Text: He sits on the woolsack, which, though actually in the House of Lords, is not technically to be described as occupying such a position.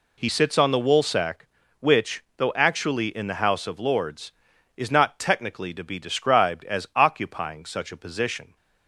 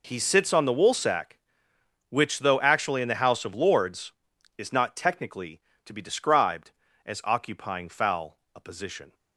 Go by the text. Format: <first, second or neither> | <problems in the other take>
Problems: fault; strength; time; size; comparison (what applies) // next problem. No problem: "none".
first | says "foul" for "such"; at 7.8 s